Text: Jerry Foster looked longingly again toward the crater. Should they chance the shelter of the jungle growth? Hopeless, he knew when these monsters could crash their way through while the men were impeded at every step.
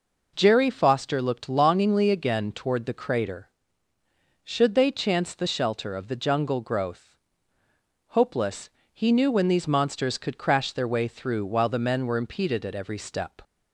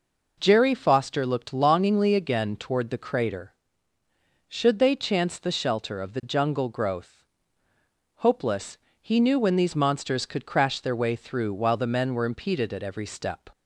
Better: neither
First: none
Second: none

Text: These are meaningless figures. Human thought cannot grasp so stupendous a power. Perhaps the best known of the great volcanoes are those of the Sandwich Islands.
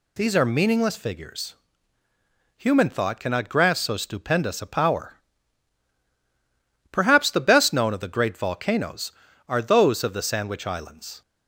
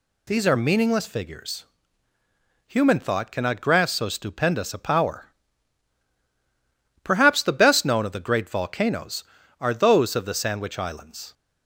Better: neither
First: none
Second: none

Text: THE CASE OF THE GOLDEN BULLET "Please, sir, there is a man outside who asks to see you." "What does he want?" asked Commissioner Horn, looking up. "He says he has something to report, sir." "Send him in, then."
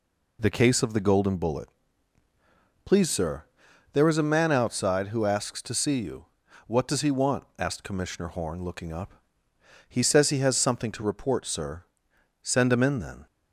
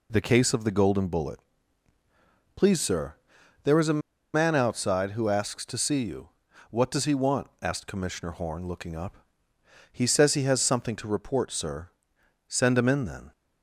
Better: first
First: pauses between "BULLET" and "Please"; at 1.6 s; 1.1 s long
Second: pauses between "BULLET" and "Please"; at 1.3 s; 1.1 s long // pauses between "a" and "man"; slight; at 4.0 s; 0.34 s long

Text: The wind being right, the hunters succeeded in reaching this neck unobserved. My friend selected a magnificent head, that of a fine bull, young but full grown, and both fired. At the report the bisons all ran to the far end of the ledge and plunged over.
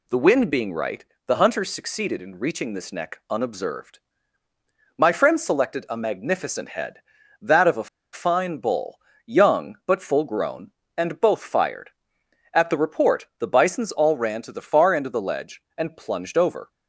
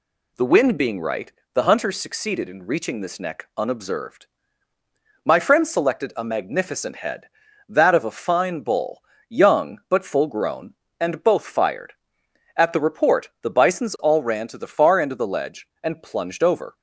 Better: second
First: pauses between "a" and "fine"; slight; at 7.8 s; 0.25 s long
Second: none

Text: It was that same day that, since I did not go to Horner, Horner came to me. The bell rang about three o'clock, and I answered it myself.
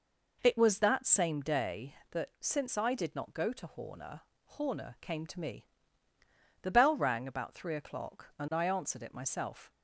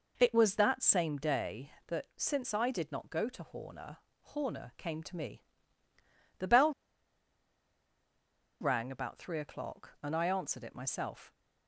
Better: first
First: none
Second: pauses between "bell" and "rang"; strong; at 6.7 s; 1.8 s long

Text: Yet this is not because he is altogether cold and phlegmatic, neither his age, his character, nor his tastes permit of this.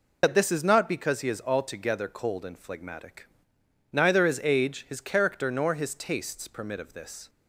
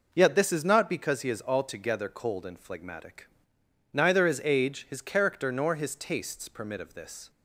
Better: second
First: loses the start of "Yet"; at 0.2 s; 100 ms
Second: none

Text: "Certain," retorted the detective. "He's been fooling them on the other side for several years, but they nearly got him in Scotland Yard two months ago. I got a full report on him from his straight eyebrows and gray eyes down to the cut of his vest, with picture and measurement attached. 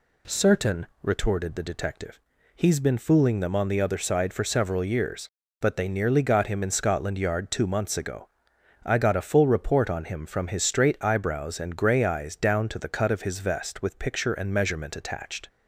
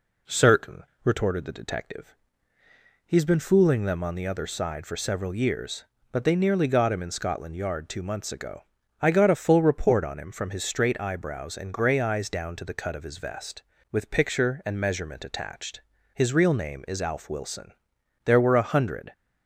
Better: first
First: none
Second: goes on to say "His real name is Alf Wilson there were a hundred"; strong; from 16.1 s on; 2.9 s long

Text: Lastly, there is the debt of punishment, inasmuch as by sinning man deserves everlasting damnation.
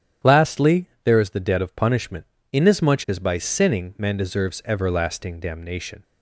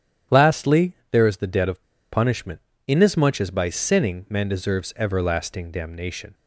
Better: first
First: starts louder than the rest; strong; until 1.4 s; 10 dB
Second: starts louder than the rest; strong; until 1.4 s; 10 dB // pauses between "of" and "punishment"; slight; at 1.8 s; 0.30 s long

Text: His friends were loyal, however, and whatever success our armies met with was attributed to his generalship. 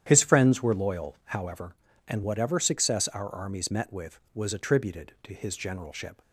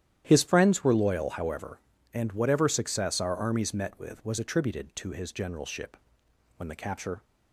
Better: first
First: starts louder than the rest; strong; until 1.0 s; 10 dB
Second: starts louder than the rest; strong; until 1.2 s; 11 dB // goes on to say "When the capture"; noticeable; from 6.5 s on; 0.68 s long

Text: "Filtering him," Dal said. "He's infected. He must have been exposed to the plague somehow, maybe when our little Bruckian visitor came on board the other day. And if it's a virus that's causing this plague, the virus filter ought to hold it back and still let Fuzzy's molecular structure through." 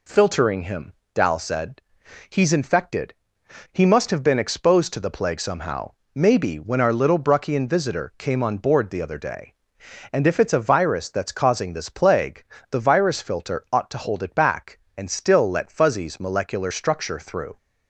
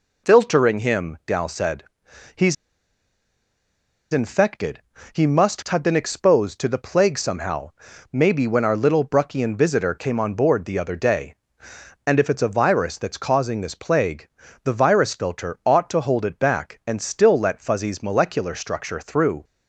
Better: first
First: none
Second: pauses between "He's" and "infected"; strong; at 2.5 s; 1.5 s long

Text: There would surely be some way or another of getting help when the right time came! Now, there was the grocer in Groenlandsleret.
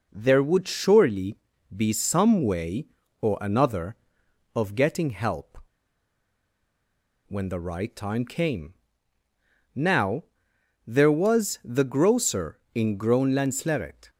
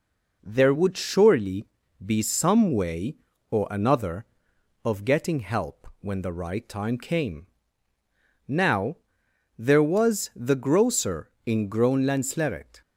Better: second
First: pauses between "surely" and "be"; at 1.3 s; 0.38 s long // pauses between "help" and "when"; strong; at 5.5 s; 1.7 s long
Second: pauses between "surely" and "be"; at 1.6 s; 0.38 s long

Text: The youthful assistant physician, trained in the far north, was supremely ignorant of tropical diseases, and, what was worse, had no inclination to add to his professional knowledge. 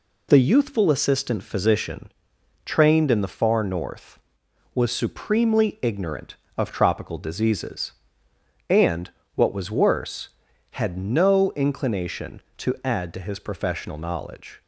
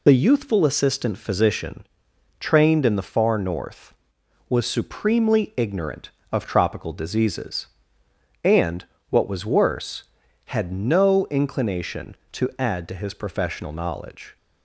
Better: first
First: none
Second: loses the start of "The"; at 0.0 s; 30 ms

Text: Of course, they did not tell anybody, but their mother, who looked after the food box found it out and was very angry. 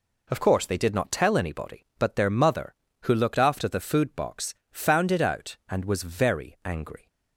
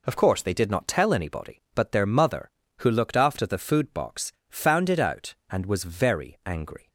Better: neither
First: pauses between "box" and "found"; slight; at 4.5 s; 0.18 s long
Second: pauses between "box" and "found"; slight; at 4.3 s; 0.18 s long

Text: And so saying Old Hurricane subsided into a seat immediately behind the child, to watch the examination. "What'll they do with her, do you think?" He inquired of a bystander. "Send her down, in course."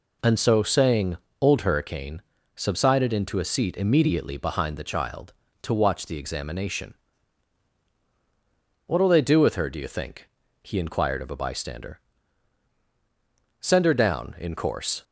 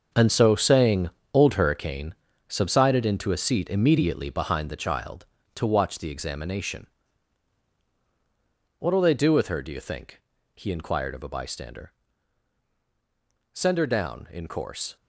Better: first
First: pauses between "saying" and "Old"; slight; at 1.1 s; 0.22 s long // pauses between "Hurricane" and "subsided"; slight; at 2.2 s; 0.34 s long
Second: gets quieter; strong; throughout; 10.5 dB // pauses between "saying" and "Old"; slight; at 1.0 s; 0.22 s long // pauses between "Hurricane" and "subsided"; slight; at 2.1 s; 0.34 s long

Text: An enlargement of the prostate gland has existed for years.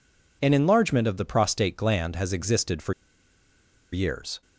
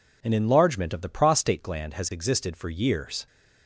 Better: second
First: pauses between "for" and "years"; at 2.9 s; 0.99 s long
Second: none

